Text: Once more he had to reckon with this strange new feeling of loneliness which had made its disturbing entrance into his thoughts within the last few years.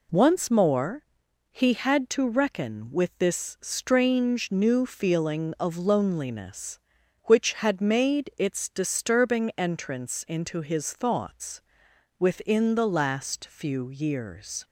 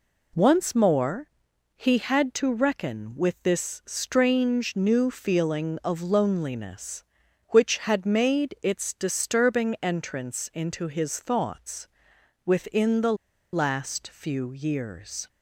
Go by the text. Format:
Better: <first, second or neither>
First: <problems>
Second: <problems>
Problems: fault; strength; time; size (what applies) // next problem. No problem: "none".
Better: first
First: pauses between "more" and "he"; noticeable; at 1.0 s; 0.48 s long // pauses between "thoughts" and "within"; noticeable; at 11.5 s; 0.58 s long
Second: pauses between "more" and "he"; noticeable; at 1.2 s; 0.48 s long // pauses between "thoughts" and "within"; noticeable; at 11.8 s; 0.58 s long // pauses between "the" and "last"; at 13.1 s; 0.39 s long